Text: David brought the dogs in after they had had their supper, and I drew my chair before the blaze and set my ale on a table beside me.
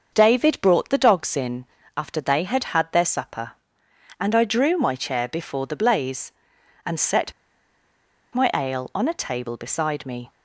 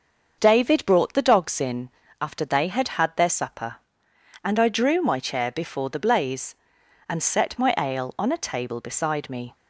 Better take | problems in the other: second | starts louder than the rest; until 1.1 s; 6.5 dB; also in the second // pauses between "in" and "after"; slight; at 1.6 s; 0.32 s long; slight in the second // pauses between "set" and "my"; at 7.3 s; 1.0 s long

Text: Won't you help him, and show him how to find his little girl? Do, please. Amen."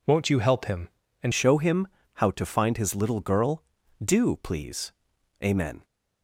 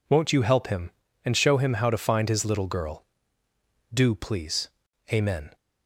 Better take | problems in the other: second | changes voice at "show"; from 1.3 s on; 4.5 s long // pauses between "him" and "how"; slight; at 1.8 s; 0.28 s long

